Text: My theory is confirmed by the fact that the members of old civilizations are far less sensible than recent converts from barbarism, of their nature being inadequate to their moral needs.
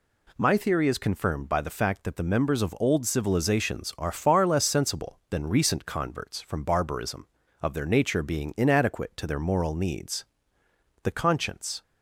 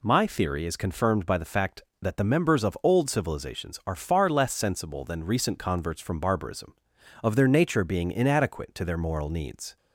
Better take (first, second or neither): second